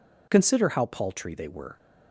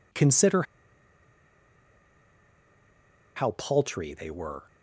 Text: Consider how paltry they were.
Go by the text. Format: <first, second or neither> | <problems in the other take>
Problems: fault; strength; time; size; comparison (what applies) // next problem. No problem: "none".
first | pauses between "Consider" and "how"; strong; at 0.6 s; 2.7 s long